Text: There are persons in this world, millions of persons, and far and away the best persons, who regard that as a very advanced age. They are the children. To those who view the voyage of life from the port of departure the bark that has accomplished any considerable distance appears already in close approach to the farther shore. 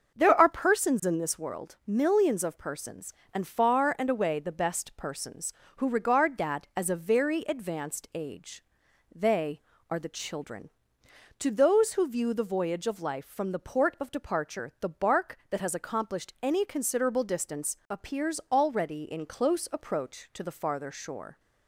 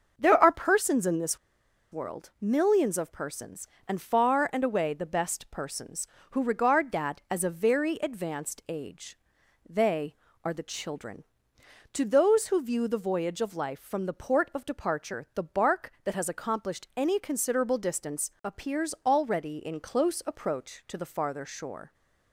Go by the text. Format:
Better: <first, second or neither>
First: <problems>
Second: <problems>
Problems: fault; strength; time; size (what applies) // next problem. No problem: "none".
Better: first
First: starts louder than the rest; until 1.2 s; 6.5 dB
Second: starts louder than the rest; until 1.1 s; 6.5 dB // pauses between "this" and "world"; noticeable; at 1.3 s; 0.53 s long